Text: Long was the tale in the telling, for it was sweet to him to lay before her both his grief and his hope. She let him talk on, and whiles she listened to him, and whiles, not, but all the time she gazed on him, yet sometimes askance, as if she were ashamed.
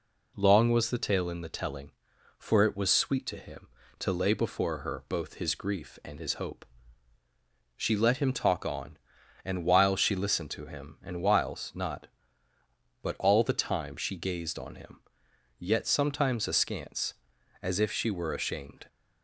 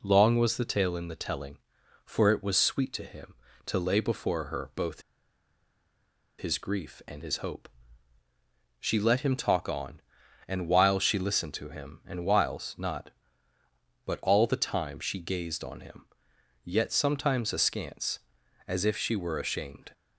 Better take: first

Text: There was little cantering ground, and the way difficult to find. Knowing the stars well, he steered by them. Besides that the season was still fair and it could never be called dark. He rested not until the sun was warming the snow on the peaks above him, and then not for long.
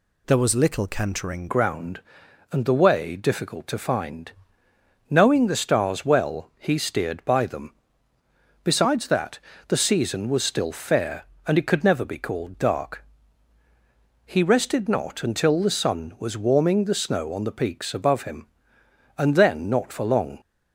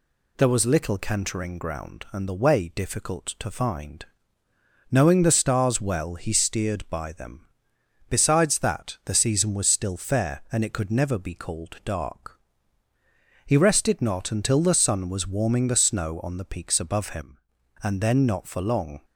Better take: second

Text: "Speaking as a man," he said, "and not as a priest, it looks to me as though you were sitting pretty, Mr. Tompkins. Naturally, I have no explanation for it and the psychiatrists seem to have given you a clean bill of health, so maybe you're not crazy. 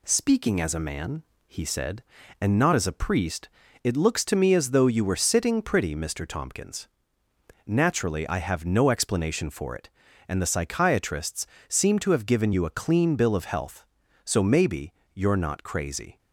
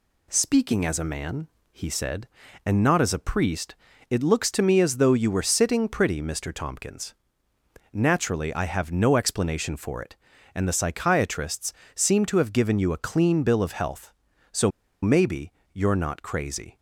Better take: first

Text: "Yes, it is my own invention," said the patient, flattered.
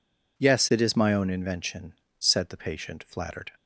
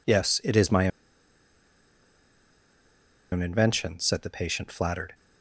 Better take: first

